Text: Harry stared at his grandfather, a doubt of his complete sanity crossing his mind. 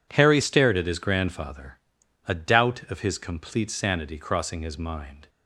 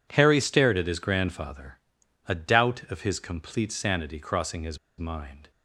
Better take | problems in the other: first | pauses between "his" and "mind"; slight; at 4.7 s; 0.20 s long

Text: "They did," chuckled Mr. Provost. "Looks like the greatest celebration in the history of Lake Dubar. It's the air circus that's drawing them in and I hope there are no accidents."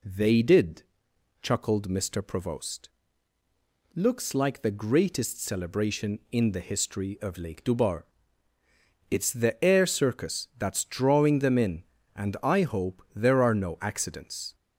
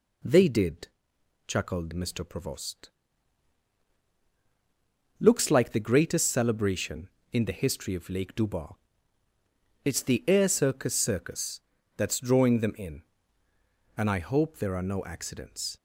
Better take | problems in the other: first | says "circus" twice; at 10.9 s

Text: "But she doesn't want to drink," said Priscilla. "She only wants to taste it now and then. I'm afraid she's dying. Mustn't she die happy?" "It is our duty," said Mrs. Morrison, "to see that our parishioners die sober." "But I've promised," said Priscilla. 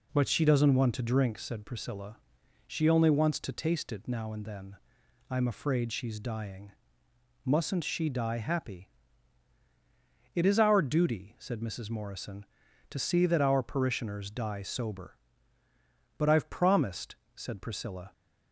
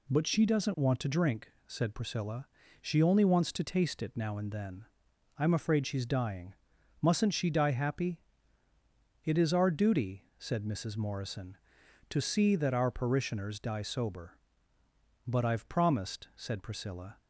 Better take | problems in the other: neither | none

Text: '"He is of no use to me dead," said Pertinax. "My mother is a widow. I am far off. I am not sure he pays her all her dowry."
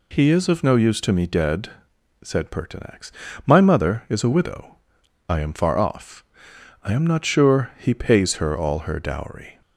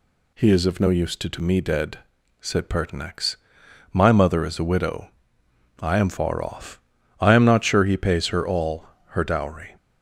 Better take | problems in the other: first | says "to" twice; at 1.2 s // pauses between "all" and "her"; slight; at 8.8 s; 0.22 s long

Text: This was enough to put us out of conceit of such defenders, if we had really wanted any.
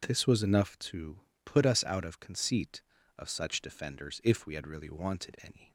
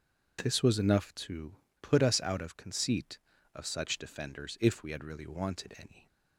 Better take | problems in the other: neither | pauses between "to" and "put"; slight; the same in both

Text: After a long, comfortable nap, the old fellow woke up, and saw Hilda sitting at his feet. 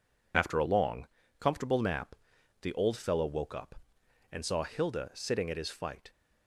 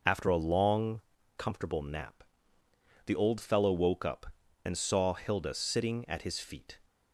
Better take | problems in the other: second | says "fight" for "feet"; at 5.6 s

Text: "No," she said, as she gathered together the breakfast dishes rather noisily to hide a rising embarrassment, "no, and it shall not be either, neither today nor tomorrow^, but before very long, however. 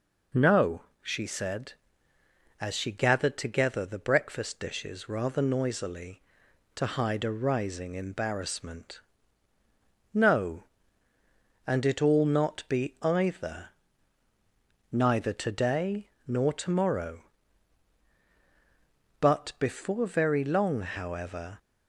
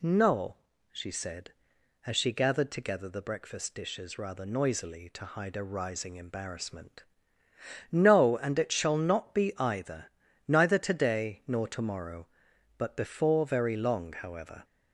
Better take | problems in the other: second | says "all" for "shall"; at 11.9 s // pauses between "today" and "nor"; slight; at 16.0 s; 0.18 s long

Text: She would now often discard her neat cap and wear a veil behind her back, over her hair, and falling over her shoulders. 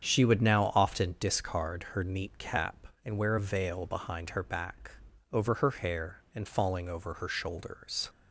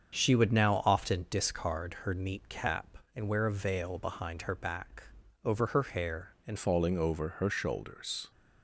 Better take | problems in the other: first | starts louder than the rest; strong; until 1.1 s; 7 dB; strong in the first // changes voice at "falling"; from 6.5 s on; 1.8 s long

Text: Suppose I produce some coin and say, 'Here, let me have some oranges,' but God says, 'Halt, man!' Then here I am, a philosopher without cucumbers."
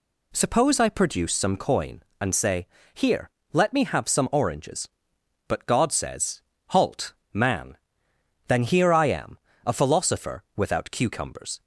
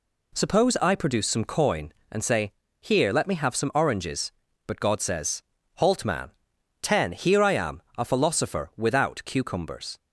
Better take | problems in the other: first | says "Ten" for "Then"; at 6.8 s

